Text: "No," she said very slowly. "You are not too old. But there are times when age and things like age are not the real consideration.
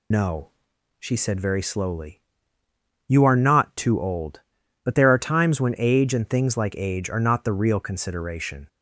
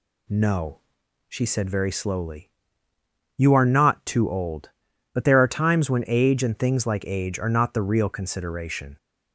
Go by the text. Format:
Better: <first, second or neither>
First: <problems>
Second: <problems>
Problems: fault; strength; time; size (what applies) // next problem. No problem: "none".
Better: second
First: loses the start of "No"; at 0.1 s; 110 ms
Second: none